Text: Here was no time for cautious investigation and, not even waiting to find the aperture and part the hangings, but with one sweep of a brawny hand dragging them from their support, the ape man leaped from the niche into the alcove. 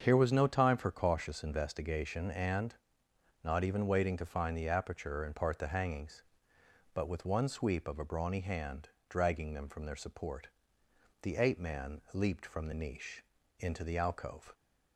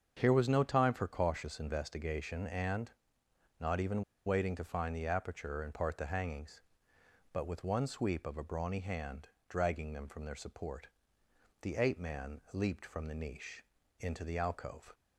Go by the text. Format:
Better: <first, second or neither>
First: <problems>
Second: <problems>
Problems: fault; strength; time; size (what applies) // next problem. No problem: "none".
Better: first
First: starts louder than the rest; until 1.0 s; 7 dB // pauses between "hand" and "dragging"; slight; at 8.8 s; 0.22 s long // pauses between "niche" and "into"; slight; at 13.2 s; 0.36 s long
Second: starts louder than the rest; until 1.2 s; 7 dB // pauses between "even" and "waiting"; slight; at 4.0 s; 0.24 s long // pauses between "hand" and "dragging"; slight; at 9.2 s; 0.22 s long // pauses between "niche" and "into"; slight; at 13.6 s; 0.36 s long